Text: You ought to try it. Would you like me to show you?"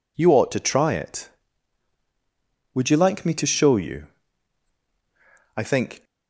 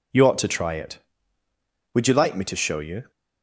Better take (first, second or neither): second